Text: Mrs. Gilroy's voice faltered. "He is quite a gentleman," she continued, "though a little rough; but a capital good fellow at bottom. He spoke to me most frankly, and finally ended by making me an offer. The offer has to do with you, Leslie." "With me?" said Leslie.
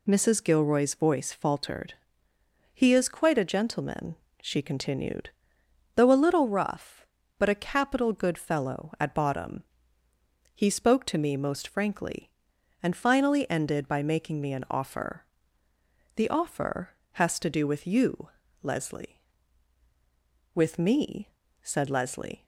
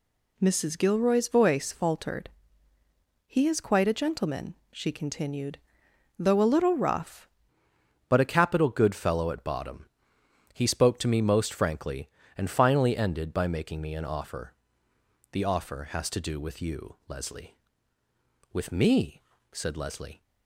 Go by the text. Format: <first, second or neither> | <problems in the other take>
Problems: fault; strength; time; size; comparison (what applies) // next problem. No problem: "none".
first | changes voice at "but"; from 8.0 s on; 12.1 s long